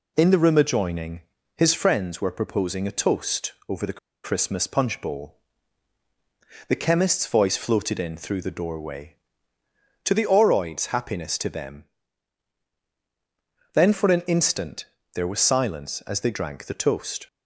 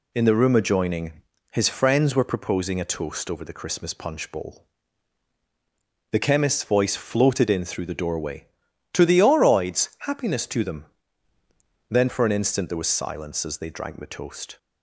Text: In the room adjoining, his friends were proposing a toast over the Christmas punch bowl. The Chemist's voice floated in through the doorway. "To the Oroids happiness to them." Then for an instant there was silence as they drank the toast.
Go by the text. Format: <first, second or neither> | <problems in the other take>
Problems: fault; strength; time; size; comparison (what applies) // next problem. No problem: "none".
second | pauses between "toast" and "over"; slight; at 3.5 s; 0.16 s long // pauses between "the" and "Christmas"; slight; at 3.9 s; 0.25 s long // pauses between "instant" and "there"; slight; at 14.8 s; 0.28 s long